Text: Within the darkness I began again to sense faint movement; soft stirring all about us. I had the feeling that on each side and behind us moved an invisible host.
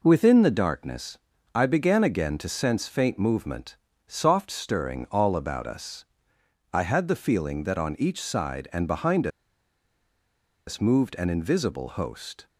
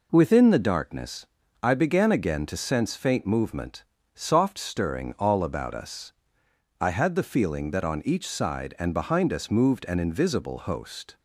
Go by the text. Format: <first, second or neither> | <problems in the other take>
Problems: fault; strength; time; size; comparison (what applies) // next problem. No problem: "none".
second | pauses between "darkness" and "I"; slight; at 1.1 s; 0.34 s long; slight in the second // pauses between "behind" and "us"; strong; at 9.2 s; 1.3 s long